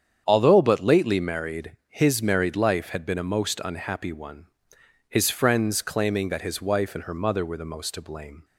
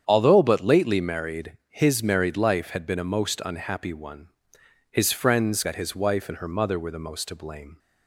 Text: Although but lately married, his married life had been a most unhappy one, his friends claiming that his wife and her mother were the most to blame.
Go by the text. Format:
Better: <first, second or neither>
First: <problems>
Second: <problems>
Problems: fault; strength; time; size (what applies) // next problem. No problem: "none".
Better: first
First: starts louder than the rest; strong; until 1.2 s; 8 dB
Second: starts louder than the rest; strong; until 1.0 s; 8 dB // skips "claiming"; at 5.6 s